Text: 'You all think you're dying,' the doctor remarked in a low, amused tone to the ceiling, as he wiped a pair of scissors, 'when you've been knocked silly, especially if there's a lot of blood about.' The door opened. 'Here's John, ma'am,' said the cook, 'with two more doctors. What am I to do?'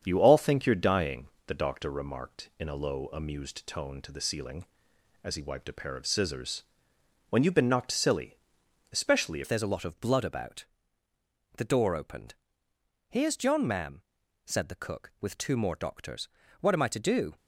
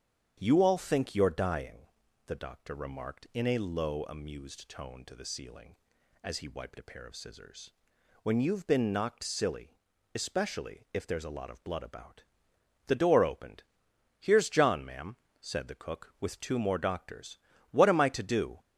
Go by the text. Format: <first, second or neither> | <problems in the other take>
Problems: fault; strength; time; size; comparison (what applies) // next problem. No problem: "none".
second | starts louder than the rest; strong; until 1.0 s; 7.5 dB; strong in the second // changes voice at "if"; from 9.4 s on; 7.9 s long